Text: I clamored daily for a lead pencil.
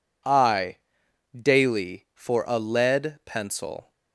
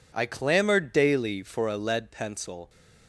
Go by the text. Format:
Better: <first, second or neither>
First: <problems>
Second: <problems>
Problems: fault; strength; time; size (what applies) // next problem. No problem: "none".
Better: second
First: skips "clamored"; at 1.0 s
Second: none